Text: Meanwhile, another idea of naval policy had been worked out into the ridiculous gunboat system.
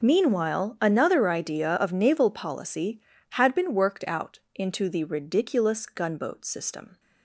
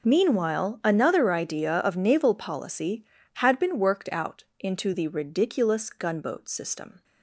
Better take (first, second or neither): neither